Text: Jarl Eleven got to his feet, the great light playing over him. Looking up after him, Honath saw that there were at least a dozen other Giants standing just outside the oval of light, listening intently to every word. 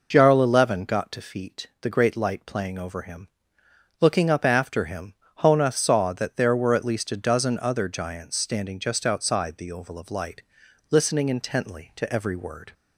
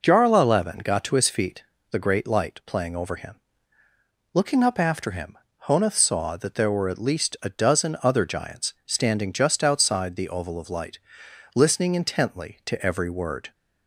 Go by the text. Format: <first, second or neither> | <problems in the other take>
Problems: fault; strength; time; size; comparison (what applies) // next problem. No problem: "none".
second | skips "his"; at 1.2 s